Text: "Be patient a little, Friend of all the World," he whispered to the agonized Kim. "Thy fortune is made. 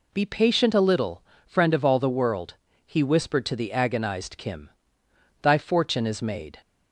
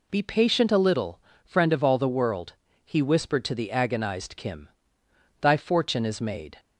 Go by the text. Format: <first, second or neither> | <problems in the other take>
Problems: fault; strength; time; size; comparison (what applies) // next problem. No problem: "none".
neither | none